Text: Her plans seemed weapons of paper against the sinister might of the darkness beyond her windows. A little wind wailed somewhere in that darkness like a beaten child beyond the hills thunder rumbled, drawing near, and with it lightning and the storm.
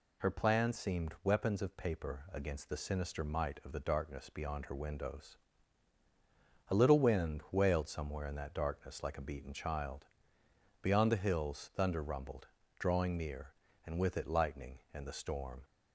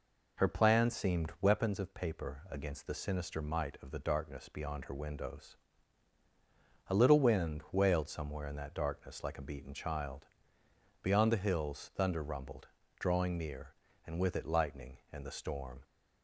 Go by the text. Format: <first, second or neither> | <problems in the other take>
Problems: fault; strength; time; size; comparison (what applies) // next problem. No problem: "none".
first | starts louder than the rest; noticeable; until 1.7 s; 5 dB // pauses between "child" and "beyond"; noticeable; at 10.2 s; 0.76 s long; noticeable in the first